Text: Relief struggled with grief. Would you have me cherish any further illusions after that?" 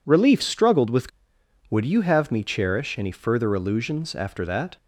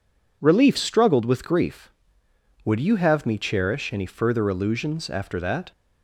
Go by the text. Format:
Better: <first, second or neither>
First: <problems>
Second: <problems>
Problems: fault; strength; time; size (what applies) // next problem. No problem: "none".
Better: second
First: skips "grief"; at 1.4 s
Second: none